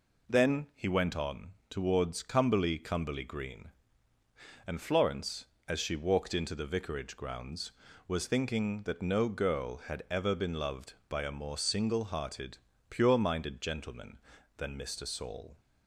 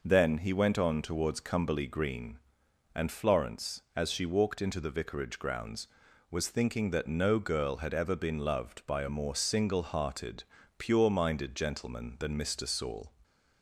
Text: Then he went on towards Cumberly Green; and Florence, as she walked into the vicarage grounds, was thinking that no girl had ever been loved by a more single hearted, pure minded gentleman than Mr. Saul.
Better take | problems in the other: second | pauses between "on" and "towards"; slight; at 1.5 s; 0.16 s long // says "Cumberly" twice; at 2.7 s

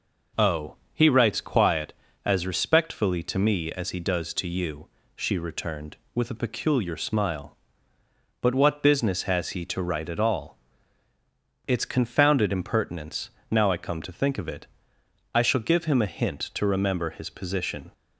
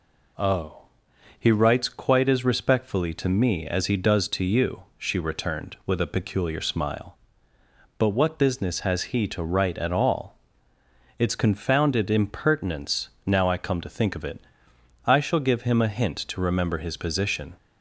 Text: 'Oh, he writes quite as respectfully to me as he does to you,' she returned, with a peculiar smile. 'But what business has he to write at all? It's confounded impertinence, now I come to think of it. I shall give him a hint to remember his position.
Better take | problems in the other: second | says "quiet" for "quite"; at 1.4 s

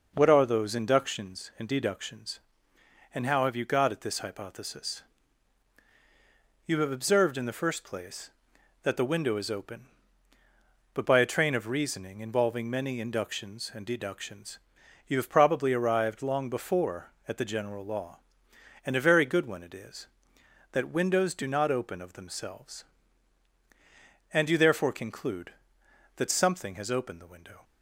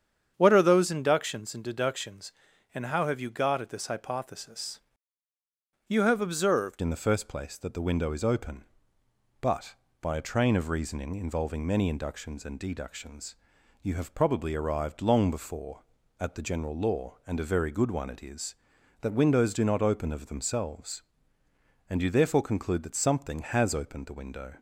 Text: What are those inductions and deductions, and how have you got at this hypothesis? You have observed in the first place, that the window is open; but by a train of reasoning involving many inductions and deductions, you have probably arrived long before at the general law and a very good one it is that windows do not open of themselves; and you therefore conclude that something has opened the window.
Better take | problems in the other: first | starts louder than the rest; strong; until 1.3 s; 8 dB // changes voice at "in"; from 6.8 s on; 17.7 s long

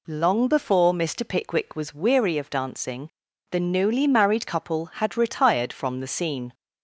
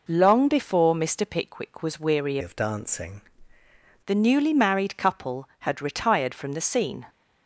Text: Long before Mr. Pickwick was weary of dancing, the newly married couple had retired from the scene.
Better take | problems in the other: first | changes voice from "of" to "dancing"; from 2.4 to 3.2 s; 0.8 s long

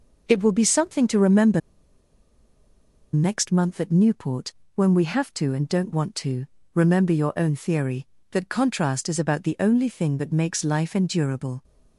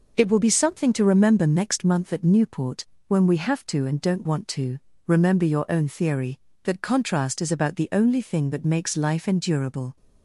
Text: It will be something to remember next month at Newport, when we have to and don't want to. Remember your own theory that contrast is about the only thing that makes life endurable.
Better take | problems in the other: second | pauses between "remember" and "next"; strong; at 1.6 s; 1.5 s long

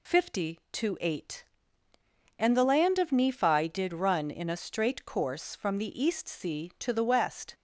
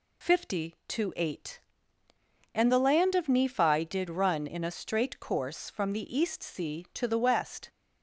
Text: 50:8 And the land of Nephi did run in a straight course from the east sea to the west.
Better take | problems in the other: neither | none

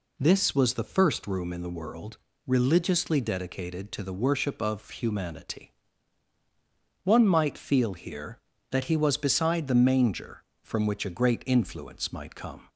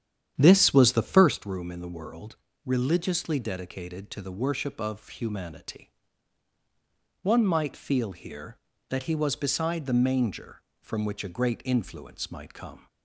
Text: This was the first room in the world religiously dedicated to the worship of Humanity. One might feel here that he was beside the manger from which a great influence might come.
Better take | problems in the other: first | starts louder than the rest; strong; until 1.4 s; 9.5 dB // pauses between "world" and "religiously"; slight; at 2.3 s; 0.28 s long; slight in the first

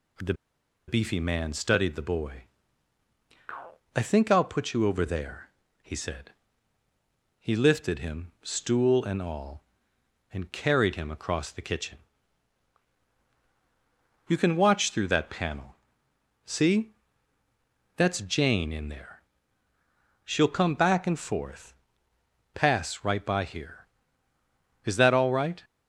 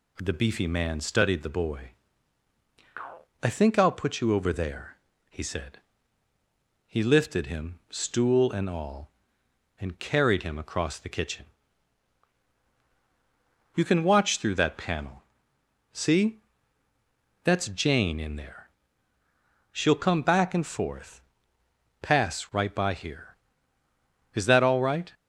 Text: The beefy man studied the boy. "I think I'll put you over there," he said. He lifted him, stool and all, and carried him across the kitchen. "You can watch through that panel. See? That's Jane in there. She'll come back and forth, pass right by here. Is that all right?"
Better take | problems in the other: second | pauses between "The" and "beefy"; noticeable; at 0.3 s; 0.54 s long

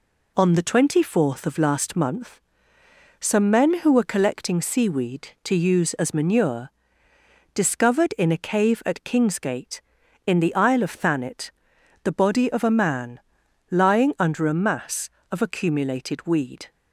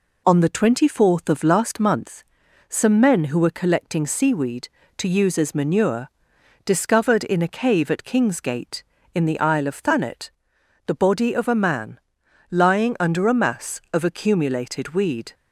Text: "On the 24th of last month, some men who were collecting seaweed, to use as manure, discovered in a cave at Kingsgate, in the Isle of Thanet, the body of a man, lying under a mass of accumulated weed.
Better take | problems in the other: neither | none

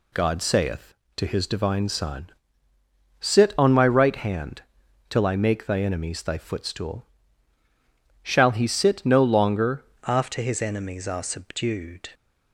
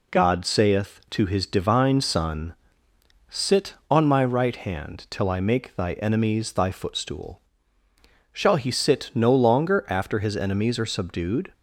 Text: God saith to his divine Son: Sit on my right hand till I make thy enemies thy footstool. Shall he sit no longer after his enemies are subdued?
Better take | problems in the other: second | pauses between "hand" and "till"; noticeable; at 4.6 s; 0.48 s long // changes voice at "after"; from 10.0 s on; 2.0 s long

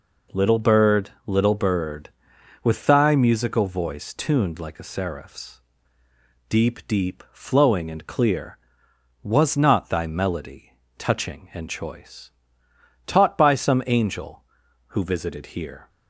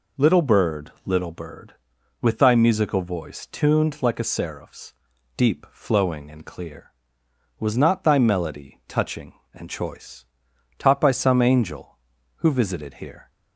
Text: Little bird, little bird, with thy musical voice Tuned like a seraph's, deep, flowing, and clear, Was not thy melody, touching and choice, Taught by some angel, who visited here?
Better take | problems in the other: second | says "deep" twice; at 6.8 s

